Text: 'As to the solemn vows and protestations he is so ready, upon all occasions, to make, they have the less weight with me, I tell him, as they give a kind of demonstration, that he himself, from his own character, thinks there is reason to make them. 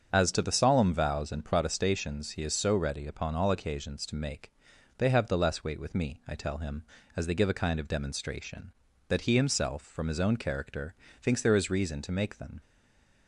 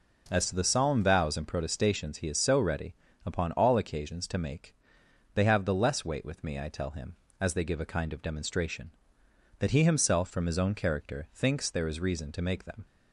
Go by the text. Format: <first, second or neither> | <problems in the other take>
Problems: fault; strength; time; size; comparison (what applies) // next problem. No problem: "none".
second | starts louder than the rest; strong; until 1.1 s; 7.5 dB // stays silent after the last word; slight; from 12.6 s on; 0.6 s long